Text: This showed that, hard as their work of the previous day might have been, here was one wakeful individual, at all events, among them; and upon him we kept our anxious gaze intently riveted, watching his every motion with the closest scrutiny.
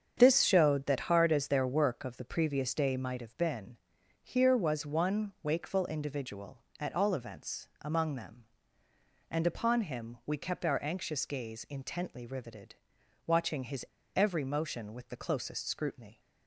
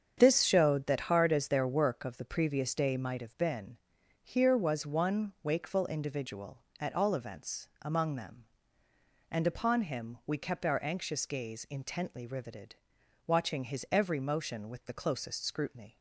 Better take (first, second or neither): second